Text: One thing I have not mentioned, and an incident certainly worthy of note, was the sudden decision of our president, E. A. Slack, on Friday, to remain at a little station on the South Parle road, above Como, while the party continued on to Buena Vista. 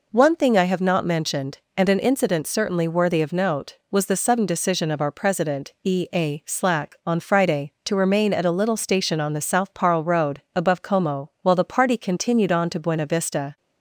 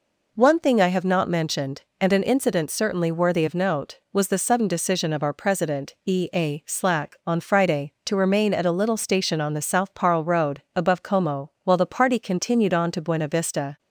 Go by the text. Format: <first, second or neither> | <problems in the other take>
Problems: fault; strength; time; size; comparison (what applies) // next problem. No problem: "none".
neither | none